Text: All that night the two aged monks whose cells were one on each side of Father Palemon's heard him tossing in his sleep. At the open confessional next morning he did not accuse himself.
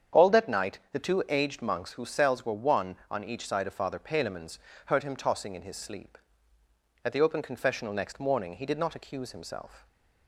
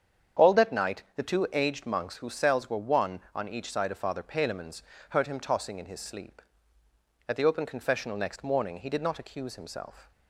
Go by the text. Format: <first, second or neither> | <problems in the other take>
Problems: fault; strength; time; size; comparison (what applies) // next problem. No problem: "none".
neither | starts louder than the rest; strong; the same in both // pauses between "Palemon's" and "heard"; slight; the same in both